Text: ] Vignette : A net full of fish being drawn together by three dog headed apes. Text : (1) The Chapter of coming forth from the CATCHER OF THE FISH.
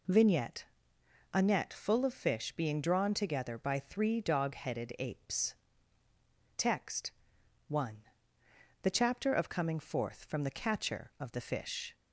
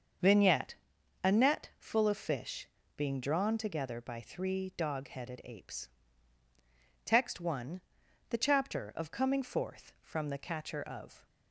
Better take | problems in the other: first | starts louder than the rest; until 1.6 s; 6.5 dB // pauses between "fish" and "being"; slight; at 2.6 s; 0.28 s long // stops before "THE FISH"; at 11.2 s

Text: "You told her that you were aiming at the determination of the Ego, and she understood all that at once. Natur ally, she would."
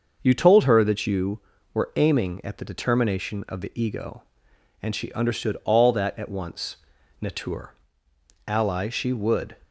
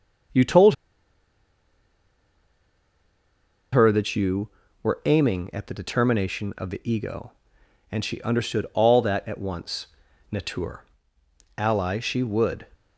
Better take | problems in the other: first | starts louder than the rest; until 4.3 s; 6 dB; also in the first // pauses between "told" and "her"; strong; at 0.7 s; 2.9 s long // pauses between "Natur" and "ally"; noticeable; at 10.8 s; 0.72 s long; noticeable in the first

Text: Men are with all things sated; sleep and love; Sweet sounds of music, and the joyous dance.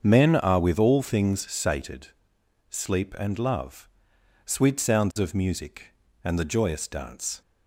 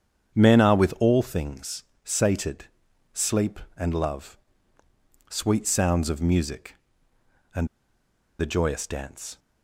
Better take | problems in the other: first | starts louder than the rest; strong; until 1.4 s; 8 dB; also in the first // pauses between "things" and "sated"; slight; at 1.8 s; 0.22 s long // pauses between "and" and "the"; noticeable; at 7.6 s; 0.72 s long

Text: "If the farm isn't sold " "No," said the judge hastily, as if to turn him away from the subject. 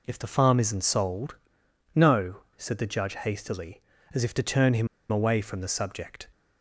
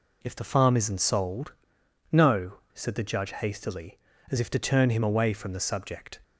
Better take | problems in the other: second | pauses between "him" and "away"; slight; at 4.8 s; 0.25 s long

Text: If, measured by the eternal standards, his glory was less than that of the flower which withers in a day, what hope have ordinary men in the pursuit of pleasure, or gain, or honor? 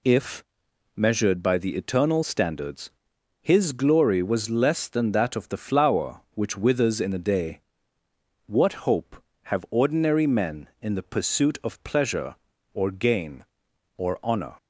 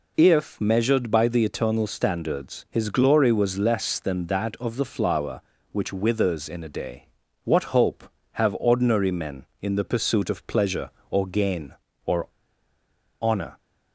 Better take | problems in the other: first | pauses between "or" and "honor"; noticeable; at 12.2 s; 0.94 s long

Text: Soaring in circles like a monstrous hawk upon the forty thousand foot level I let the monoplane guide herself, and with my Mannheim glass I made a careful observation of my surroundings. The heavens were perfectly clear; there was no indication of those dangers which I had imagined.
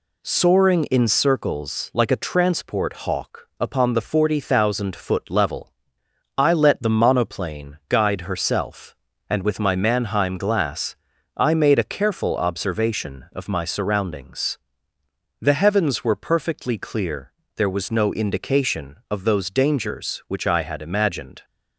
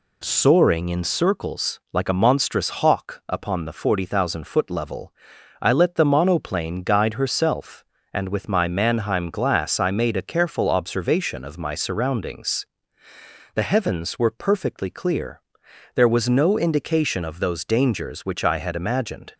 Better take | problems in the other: second | says "transport" for "monstrous"; at 2.2 s // pauses between "level" and "I"; noticeable; at 5.7 s; 0.64 s long; noticeable in the second // pauses between "glass" and "I"; at 10.9 s; 0.44 s long

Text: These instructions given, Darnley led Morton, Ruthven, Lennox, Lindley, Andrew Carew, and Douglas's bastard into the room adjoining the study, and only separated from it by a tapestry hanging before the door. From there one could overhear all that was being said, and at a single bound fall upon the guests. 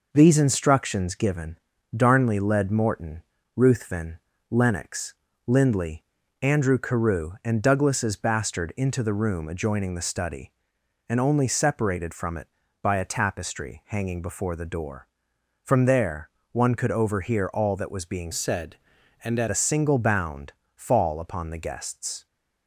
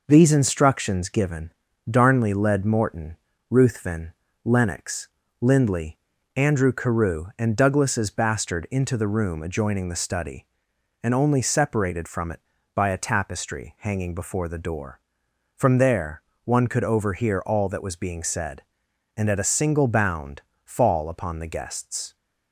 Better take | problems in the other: second | pauses between "there" and "one"; slight; at 16.2 s; 0.22 s long; slight in the second // changes voice from "said" to "at"; from 18.3 to 19.4 s; 1.1 s long // pauses between "bound" and "fall"; slight; at 20.5 s; 0.24 s long; slight in the second

